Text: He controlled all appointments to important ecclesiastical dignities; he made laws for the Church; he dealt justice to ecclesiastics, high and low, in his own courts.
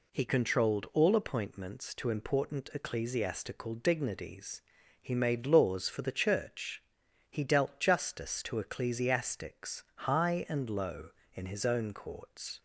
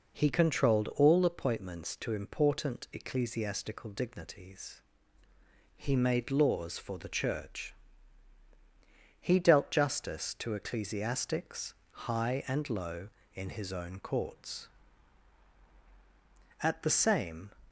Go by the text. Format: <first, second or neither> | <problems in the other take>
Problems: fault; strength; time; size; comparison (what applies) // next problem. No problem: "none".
first | goes on to say "At the same"; noticeable; from 16.6 s on; 0.90 s long